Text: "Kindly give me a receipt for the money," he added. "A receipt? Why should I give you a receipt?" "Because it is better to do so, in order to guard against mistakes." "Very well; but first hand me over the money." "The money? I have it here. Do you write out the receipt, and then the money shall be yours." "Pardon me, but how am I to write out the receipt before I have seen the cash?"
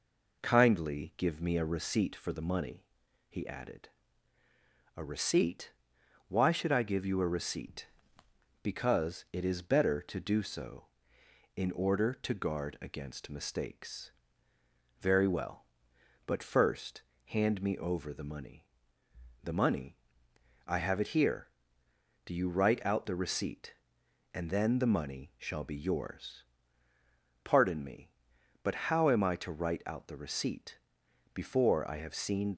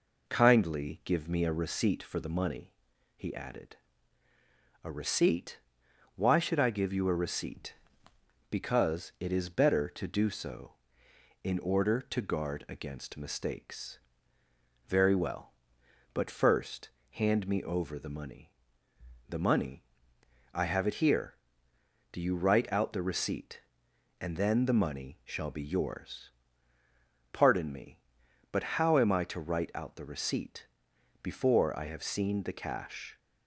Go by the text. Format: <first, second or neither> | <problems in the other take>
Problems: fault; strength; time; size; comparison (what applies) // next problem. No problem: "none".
second | pauses between "first" and "hand"; slight; at 17.0 s; 0.24 s long; slight in the second // pauses between "receipt" and "before"; noticeable; at 30.7 s; 0.58 s long; noticeable in the second // stops before "the cash"; at 32.5 s